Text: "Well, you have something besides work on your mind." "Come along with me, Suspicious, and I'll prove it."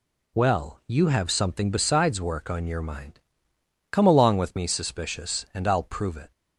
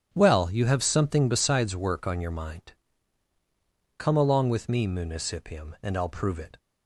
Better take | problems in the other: first | starts louder than the rest; strong; until 1.1 s; 10 dB // says "Municipium" for "Suspicious"; at 4.8 s

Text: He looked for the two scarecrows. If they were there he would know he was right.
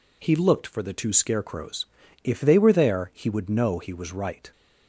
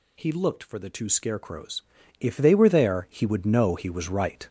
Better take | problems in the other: first | gets louder; throughout; 6.5 dB

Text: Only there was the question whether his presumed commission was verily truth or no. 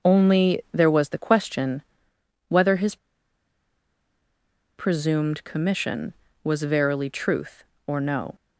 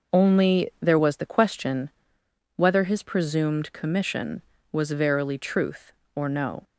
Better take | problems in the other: second | pauses between "question" and "whether"; noticeable; at 1.8 s; 0.66 s long; noticeable in the second // pauses between "his" and "presumed"; strong; at 2.9 s; 1.8 s long

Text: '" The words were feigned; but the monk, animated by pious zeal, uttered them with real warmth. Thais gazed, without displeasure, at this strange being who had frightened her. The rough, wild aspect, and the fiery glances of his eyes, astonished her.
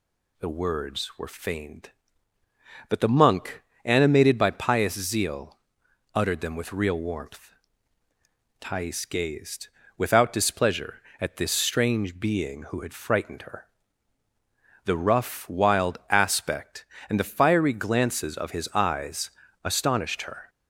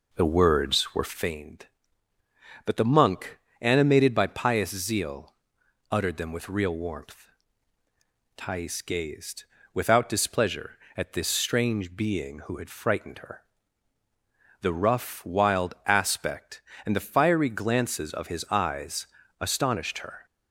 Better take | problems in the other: first | starts louder than the rest; noticeable; until 1.4 s; 4.5 dB

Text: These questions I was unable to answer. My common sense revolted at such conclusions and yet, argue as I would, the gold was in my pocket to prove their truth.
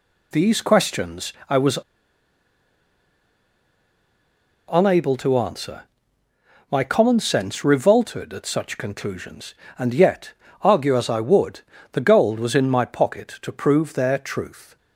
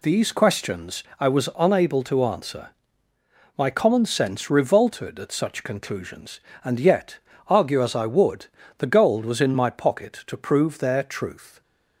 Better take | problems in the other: second | pauses between "questions" and "I"; slight; at 1.3 s; 0.18 s long; slight in the second // pauses between "was" and "unable"; strong; at 1.7 s; 2.9 s long

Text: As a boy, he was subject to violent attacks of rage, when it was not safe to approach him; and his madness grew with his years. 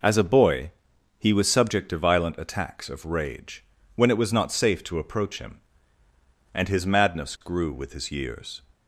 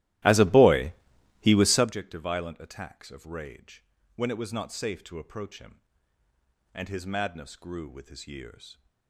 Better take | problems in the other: first | starts louder than the rest; strong; until 1.9 s; 16 dB

